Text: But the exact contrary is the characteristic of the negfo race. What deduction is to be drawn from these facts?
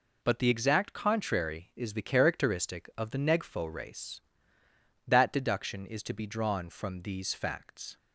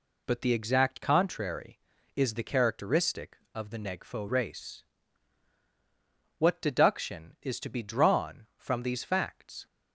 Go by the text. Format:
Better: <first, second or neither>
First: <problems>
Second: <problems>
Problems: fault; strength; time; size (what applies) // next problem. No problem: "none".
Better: second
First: says "That" for "What"; at 5.0 s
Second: none